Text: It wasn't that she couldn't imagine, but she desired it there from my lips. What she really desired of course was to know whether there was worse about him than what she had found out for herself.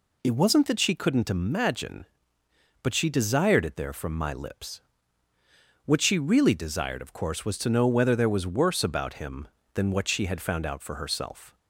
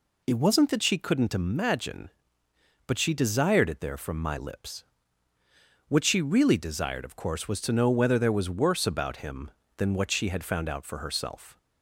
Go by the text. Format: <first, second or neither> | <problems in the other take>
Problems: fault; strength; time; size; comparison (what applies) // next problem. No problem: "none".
neither | none